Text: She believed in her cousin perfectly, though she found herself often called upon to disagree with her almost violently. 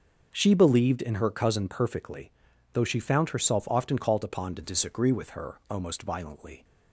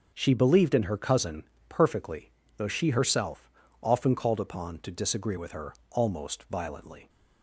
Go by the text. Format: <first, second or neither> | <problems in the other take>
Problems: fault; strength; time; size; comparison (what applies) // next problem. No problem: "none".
first | starts louder than the rest; until 1.1 s; 6.5 dB; also in the first // pauses between "cousin" and "perfectly"; slight; at 1.4 s; 0.24 s long // skips "found"; at 2.9 s // pauses between "herself" and "often"; slight; at 3.5 s; 0.32 s long // pauses between "her" and "almost"; slight; at 5.7 s; 0.18 s long